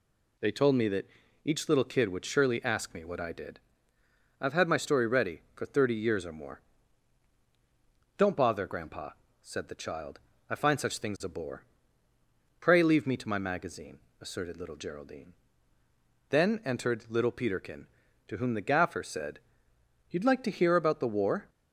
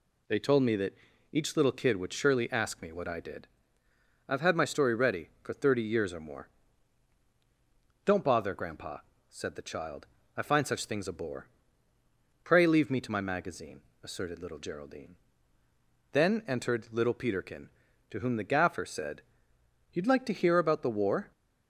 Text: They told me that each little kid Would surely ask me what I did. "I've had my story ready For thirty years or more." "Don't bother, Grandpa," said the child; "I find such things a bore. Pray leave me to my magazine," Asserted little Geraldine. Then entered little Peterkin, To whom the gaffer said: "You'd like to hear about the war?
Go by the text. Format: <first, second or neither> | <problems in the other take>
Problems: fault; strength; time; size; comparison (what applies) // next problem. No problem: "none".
neither | pauses between "that" and "each"; slight; the same in both